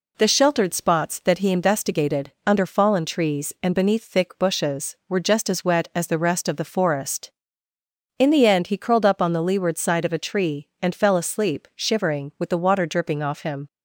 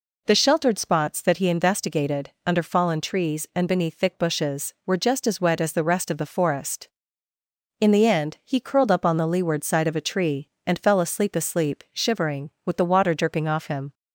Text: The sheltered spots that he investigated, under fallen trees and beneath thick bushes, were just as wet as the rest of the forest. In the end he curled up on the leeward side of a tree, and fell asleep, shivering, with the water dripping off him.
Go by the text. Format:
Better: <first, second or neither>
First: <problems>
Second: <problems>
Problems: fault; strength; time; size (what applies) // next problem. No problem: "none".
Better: first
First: none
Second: says "asleep" twice; at 11.3 s